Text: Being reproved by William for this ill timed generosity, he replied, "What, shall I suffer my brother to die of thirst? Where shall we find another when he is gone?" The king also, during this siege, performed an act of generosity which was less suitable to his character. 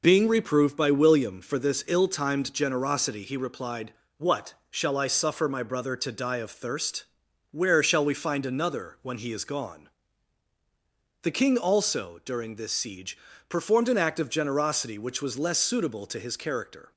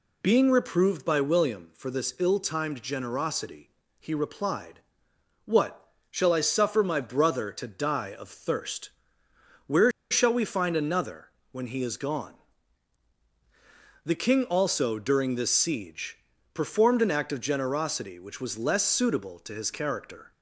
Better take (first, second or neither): first